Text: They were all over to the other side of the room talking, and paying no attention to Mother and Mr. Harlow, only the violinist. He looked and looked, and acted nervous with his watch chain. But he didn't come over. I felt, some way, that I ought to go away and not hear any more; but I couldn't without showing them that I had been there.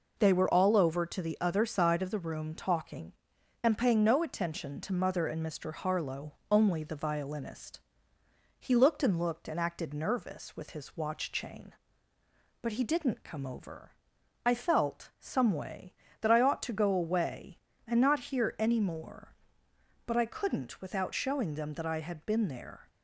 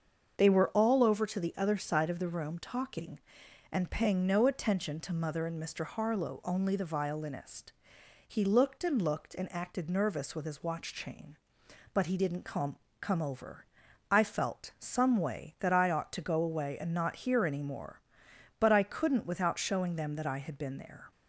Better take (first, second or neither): first